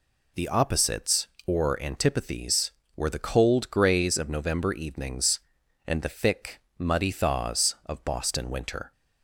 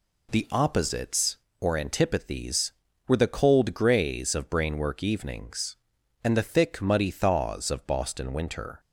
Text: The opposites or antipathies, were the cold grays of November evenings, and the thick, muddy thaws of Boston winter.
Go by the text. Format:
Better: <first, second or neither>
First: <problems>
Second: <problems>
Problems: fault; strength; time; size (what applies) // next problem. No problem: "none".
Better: first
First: none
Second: says "Brainwork" for "November"; at 4.4 s